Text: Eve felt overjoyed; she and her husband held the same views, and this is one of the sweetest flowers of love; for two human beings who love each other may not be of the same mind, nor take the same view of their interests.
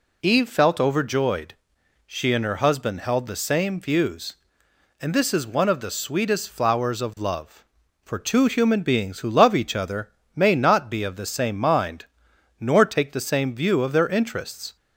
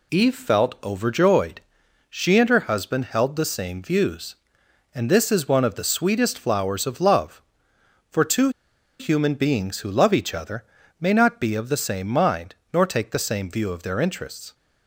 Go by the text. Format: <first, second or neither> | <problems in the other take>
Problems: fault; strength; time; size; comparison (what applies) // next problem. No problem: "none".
first | pauses between "two" and "human"; noticeable; at 8.4 s; 0.50 s long // pauses between "other" and "may"; slight; at 10.6 s; 0.34 s long; slight in the first